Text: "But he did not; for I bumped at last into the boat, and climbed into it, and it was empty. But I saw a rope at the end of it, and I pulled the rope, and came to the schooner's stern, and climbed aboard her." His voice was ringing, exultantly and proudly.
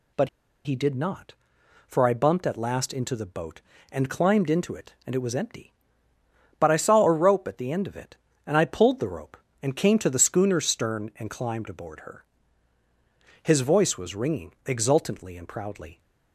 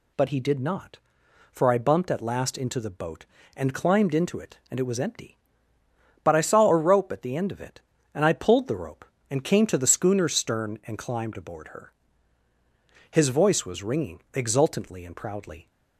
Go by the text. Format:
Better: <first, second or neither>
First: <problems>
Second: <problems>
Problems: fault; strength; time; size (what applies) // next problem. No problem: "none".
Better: second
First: pauses between "But" and "he"; slight; at 0.2 s; 0.35 s long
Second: none